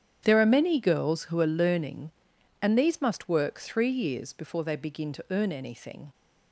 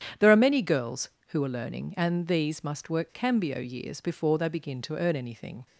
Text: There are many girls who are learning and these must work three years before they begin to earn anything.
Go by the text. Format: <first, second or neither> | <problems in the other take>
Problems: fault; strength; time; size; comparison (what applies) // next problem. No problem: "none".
first | starts louder than the rest; strong; until 1.3 s; 9.5 dB; strong in the first // says "cambio" for "three"; at 3.1 s